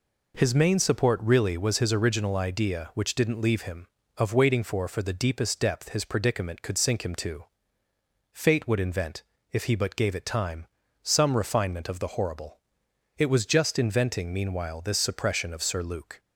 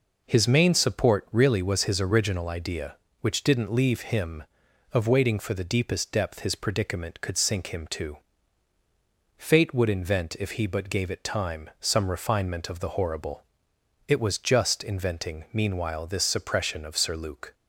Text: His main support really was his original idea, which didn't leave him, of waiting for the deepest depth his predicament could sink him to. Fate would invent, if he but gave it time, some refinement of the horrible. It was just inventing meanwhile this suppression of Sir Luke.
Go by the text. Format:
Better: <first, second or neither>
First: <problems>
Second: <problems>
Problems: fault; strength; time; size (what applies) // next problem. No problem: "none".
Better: second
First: says "for" twice; at 4.8 s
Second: none